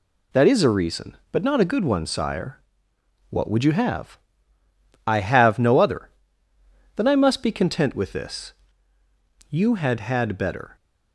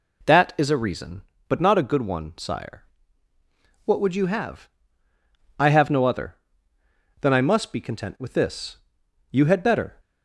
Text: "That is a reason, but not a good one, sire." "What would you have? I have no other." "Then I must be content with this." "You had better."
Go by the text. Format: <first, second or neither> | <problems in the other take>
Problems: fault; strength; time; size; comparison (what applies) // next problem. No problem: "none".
second | says "had" twice; at 10.0 s